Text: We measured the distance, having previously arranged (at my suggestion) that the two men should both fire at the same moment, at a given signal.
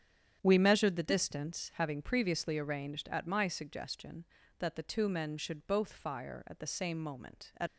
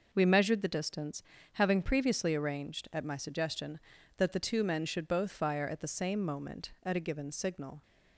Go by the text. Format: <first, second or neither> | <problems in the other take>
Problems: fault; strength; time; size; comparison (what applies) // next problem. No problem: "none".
second | starts louder than the rest; strong; until 1.4 s; 9 dB // stops before "a given signal"; at 7.6 s